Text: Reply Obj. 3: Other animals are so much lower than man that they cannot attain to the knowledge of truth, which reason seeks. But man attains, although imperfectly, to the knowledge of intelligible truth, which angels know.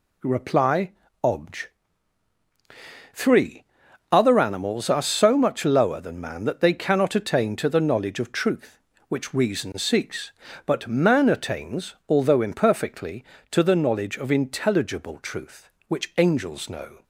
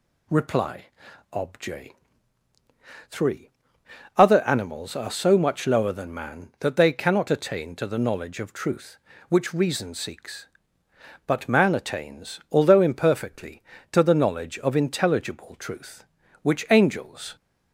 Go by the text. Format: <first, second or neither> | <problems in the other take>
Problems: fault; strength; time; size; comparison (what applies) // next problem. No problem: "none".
first | pauses between "Reply" and "Obj"; noticeable; at 0.8 s; 0.48 s long; slight in the first // stops before "know"; at 17.3 s